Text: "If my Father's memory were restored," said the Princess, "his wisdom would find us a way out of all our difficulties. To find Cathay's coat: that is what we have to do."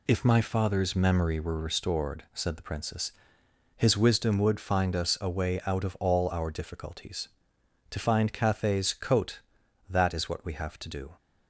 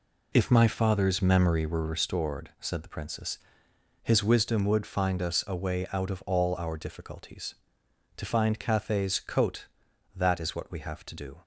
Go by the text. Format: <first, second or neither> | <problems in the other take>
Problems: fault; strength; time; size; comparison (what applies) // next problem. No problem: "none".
first | starts louder than the rest; slight; until 2.2 s; 2.5 dB